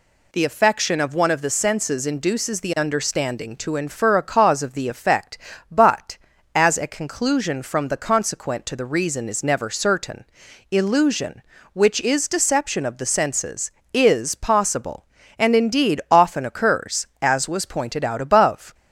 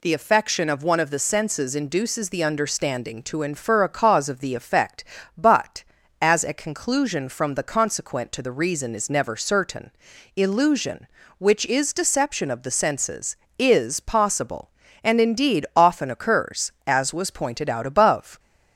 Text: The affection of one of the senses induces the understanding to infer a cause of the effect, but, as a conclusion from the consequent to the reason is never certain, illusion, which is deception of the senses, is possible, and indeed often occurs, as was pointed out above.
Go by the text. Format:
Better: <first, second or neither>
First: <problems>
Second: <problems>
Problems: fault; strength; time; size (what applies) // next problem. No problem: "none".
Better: neither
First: none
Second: none